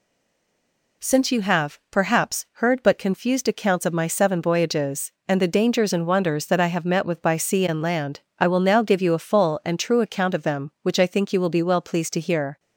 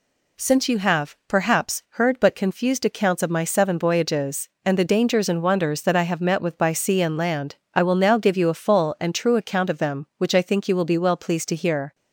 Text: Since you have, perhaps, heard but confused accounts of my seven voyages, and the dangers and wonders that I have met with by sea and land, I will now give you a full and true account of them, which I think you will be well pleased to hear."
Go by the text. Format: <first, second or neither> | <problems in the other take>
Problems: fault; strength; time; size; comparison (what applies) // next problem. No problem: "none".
second | stays silent before the first word; until 1.0 s; 1.0 s long